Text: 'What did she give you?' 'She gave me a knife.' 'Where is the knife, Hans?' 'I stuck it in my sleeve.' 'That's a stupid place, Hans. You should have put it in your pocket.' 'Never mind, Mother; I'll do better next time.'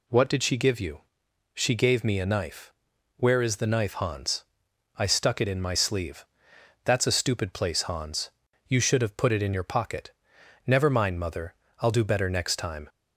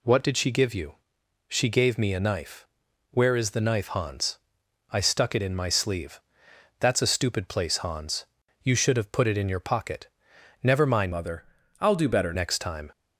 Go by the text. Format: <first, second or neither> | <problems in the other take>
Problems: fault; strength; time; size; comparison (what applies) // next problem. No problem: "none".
first | changes voice from "Mother" to "better"; from 11.1 to 12.3 s; 1.2 s long